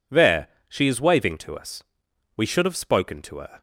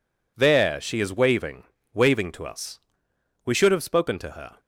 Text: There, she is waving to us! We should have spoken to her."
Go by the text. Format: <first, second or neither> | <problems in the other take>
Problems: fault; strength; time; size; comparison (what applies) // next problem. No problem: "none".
first | says "waving" twice; at 1.9 s